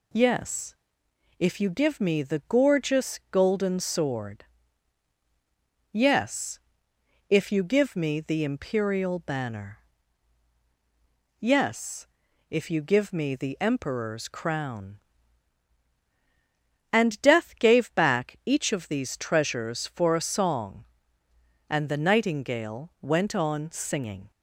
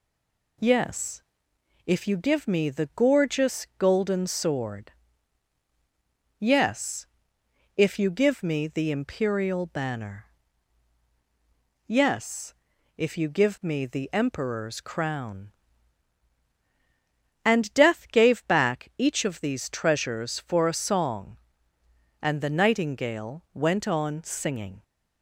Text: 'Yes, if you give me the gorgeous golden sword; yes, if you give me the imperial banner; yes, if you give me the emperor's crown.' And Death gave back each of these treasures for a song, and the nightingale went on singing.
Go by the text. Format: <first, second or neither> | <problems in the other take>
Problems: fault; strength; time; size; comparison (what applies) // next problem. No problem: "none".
first | stays silent before the first word; slight; until 0.5 s; 0.5 s long